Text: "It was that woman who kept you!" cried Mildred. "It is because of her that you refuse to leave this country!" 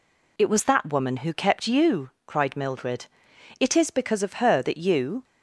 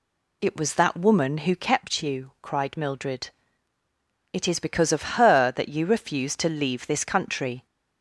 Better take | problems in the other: second | stops before "refuse to leave this country"; at 5.2 s

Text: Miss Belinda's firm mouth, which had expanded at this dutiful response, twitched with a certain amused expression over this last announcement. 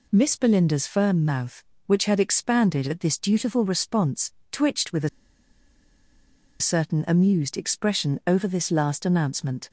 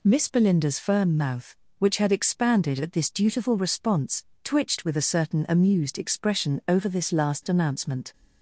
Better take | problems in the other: second | pauses between "a" and "certain"; strong; at 5.0 s; 1.5 s long

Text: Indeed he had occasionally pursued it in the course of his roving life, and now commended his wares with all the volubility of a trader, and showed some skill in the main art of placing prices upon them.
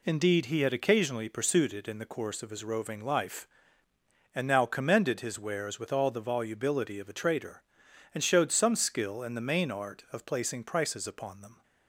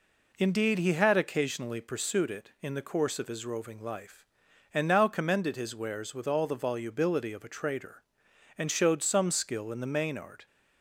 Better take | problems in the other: first | stops before "of placing prices upon them"; at 10.4 s

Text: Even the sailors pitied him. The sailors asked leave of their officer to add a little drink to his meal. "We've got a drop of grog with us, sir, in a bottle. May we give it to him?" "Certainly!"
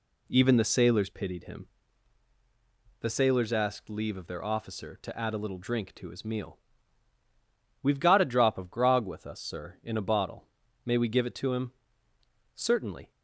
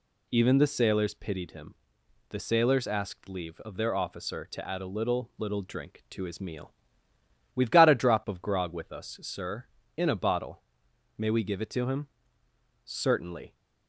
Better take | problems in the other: first | says "little" twice; at 5.3 s

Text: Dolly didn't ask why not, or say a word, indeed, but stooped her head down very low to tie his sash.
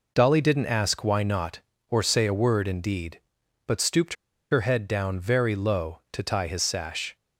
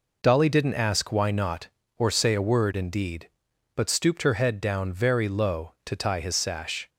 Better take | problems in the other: second | pauses between "stooped" and "her"; at 4.1 s; 0.37 s long

